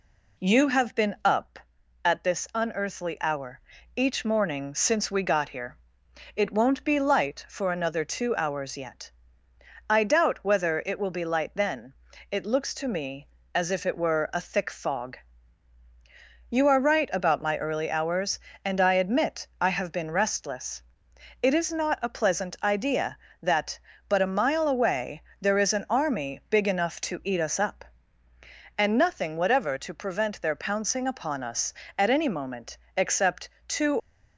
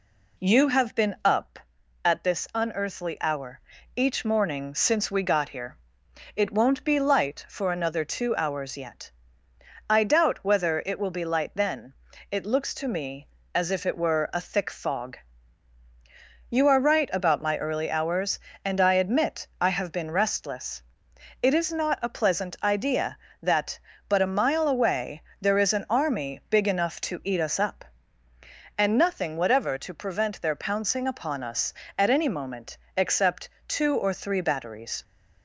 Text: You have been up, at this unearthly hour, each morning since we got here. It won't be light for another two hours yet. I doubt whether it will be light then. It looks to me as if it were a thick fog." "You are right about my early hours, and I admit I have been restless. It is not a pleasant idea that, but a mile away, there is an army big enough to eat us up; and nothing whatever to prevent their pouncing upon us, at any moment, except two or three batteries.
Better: second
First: pauses between "except" and "two"; slight; at 33.4 s; 0.18 s long // stops before "or three batteries"; at 33.9 s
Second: pauses between "except" and "two"; slight; at 33.4 s; 0.18 s long

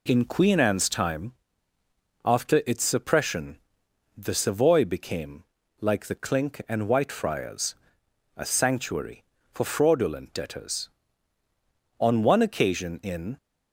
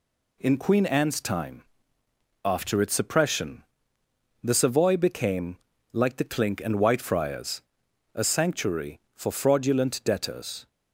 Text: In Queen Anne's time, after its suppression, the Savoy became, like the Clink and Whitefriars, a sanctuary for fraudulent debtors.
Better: second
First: goes on to say "On one occasion in"; from 11.9 s on; 1.3 s long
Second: none

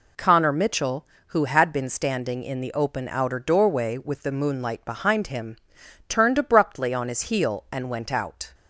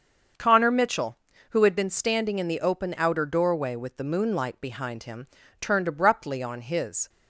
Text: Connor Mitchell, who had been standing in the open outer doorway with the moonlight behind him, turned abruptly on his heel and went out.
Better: first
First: none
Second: starts louder than the rest; until 1.7 s; 6.5 dB // stops before "heel and went out"; at 7.0 s

